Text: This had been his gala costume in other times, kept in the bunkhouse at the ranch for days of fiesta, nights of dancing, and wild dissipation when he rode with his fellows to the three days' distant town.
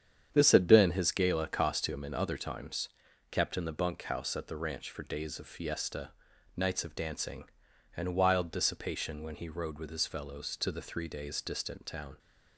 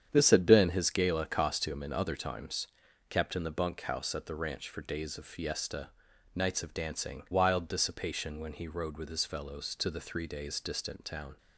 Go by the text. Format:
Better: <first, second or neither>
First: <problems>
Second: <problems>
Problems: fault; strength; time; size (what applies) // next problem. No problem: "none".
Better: first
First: starts louder than the rest; strong; until 1.3 s; 8.5 dB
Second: starts louder than the rest; strong; until 1.1 s; 8.5 dB // skips "and"; at 7.2 s